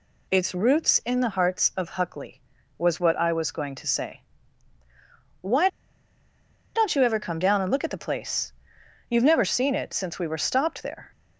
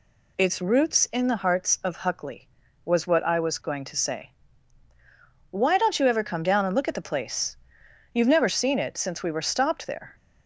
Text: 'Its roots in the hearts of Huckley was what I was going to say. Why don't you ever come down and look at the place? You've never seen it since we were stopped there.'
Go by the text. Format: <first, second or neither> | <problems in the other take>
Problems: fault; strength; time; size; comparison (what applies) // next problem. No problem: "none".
second | pauses between "Why" and "don't"; at 5.6 s; 1.0 s long